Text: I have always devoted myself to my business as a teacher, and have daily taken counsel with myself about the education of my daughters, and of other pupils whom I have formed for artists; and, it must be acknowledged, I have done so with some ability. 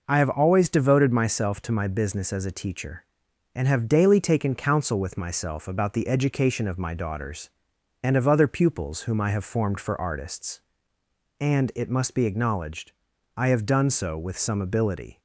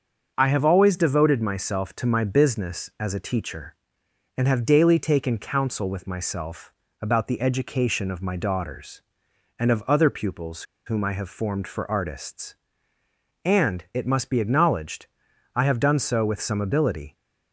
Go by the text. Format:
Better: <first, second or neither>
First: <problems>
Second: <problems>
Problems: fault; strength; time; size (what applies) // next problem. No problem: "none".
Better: first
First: none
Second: starts louder than the rest; until 1.3 s; 6.5 dB // pauses between "myself" and "about"; slight; at 6.7 s; 0.30 s long // pauses between "pupils" and "whom"; slight; at 10.6 s; 0.23 s long